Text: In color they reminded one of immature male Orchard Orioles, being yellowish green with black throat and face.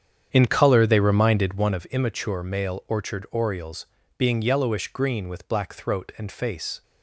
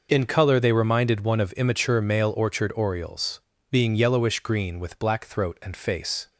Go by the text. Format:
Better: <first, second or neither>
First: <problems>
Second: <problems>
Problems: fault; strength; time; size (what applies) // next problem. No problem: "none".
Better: second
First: starts louder than the rest; strong; until 1.8 s; 8.5 dB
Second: none